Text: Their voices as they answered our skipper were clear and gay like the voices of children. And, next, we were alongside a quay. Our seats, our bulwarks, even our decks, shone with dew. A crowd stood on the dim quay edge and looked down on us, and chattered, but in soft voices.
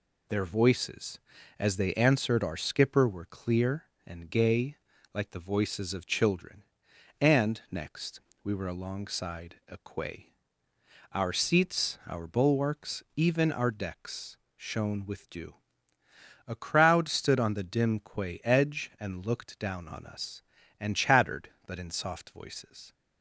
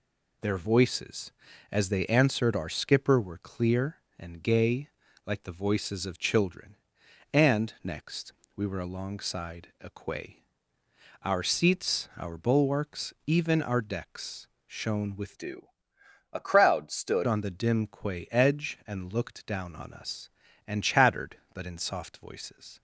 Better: first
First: pauses between "gay" and "like"; at 4.7 s; 0.38 s long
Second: pauses between "gay" and "like"; at 4.8 s; 0.38 s long // changes voice from "dew" to "stood"; from 15.3 to 17.2 s; 1.9 s long

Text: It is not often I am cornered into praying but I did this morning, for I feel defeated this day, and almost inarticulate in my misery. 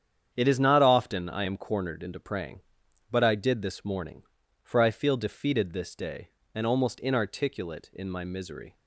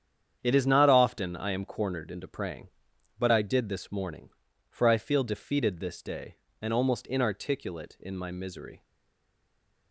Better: first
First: starts louder than the rest; strong; until 1.3 s; 8.5 dB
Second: starts louder than the rest; strong; until 1.4 s; 8.5 dB // stays silent after the last word; from 8.8 s on; 1.1 s long

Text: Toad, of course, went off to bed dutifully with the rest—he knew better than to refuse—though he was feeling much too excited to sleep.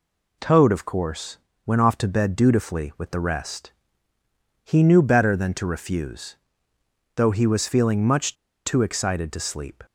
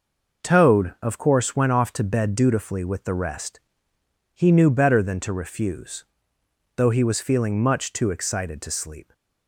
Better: second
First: pauses between "much" and "too"; slight; at 8.3 s; 0.30 s long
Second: none

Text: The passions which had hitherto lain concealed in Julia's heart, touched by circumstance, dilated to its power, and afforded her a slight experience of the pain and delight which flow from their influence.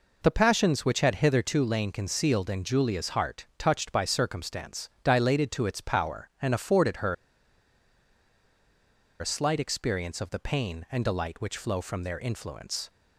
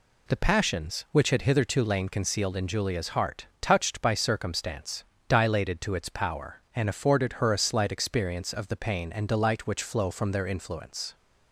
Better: second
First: pauses between "her" and "a"; strong; at 7.1 s; 2.0 s long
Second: none

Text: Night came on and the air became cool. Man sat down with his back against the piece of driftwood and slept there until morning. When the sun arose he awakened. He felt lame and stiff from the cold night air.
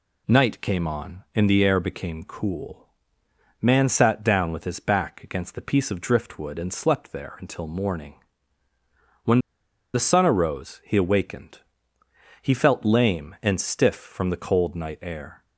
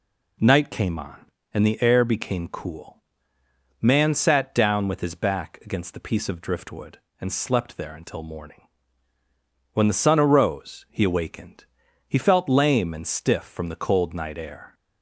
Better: second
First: pauses between "When" and "the"; noticeable; at 9.3 s; 0.55 s long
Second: none

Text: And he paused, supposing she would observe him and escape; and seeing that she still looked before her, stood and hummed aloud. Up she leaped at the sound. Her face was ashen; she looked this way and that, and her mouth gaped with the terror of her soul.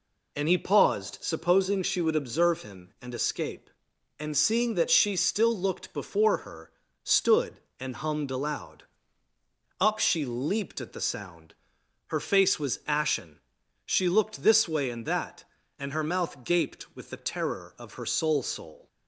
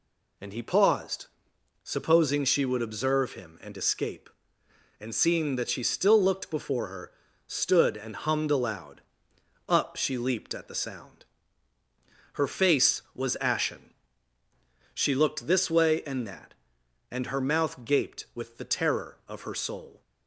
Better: second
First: says "soul" twice; at 18.4 s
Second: none

